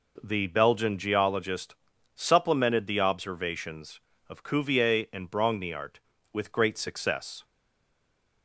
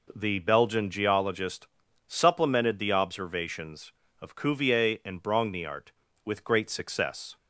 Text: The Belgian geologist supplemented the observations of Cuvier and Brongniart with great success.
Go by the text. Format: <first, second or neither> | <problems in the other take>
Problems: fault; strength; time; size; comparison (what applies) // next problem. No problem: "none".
second | pauses between "geologist" and "supplemented"; at 1.7 s; 0.40 s long; also in the second // stays silent after the last word; from 7.4 s on; 1.0 s long